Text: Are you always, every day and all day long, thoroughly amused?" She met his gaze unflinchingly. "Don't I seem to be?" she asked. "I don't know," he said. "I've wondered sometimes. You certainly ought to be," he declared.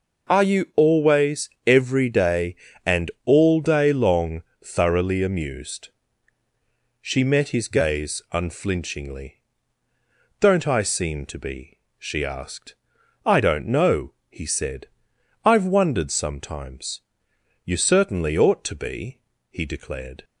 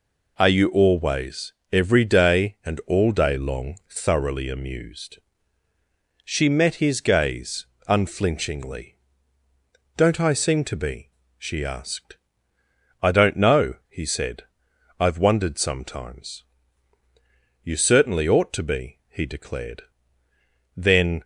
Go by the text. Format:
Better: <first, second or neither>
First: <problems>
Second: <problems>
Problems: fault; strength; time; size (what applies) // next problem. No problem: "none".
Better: first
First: none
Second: pauses between "gaze" and "unflinchingly"; slight; at 7.6 s; 0.20 s long // goes on to say "Then"; slight; from 20.7 s on; 0.48 s long